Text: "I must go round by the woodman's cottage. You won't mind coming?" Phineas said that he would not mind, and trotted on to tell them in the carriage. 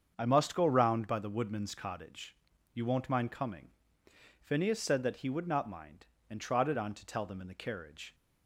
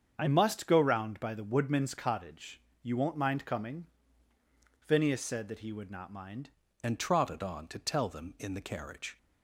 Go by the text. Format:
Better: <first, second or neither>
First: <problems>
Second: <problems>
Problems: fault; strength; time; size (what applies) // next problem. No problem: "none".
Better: first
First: starts louder than the rest; strong; until 1.1 s; 7.5 dB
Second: starts louder than the rest; strong; until 1.1 s; 7.5 dB // changes voice at "and"; from 6.8 s on; 2.3 s long